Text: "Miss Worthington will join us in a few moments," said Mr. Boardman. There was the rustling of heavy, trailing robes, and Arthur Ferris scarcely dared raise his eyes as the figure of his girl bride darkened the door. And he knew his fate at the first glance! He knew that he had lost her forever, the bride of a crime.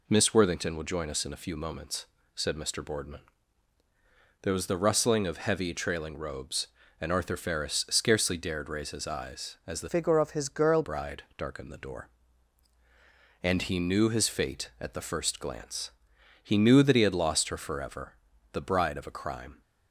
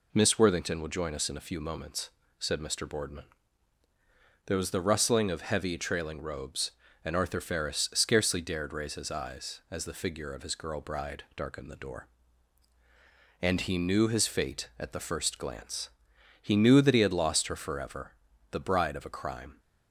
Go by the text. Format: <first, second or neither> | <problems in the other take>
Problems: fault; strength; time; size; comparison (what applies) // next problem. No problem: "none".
second | changes voice from "figure" to "girl"; from 9.9 to 10.8 s; 0.9 s long